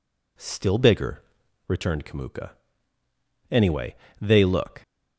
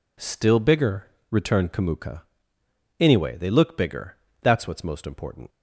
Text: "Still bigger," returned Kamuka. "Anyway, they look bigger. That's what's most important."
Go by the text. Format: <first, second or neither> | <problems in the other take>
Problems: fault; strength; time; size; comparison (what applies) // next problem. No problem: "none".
second | stops before "bigger That's what's most important"; at 4.8 s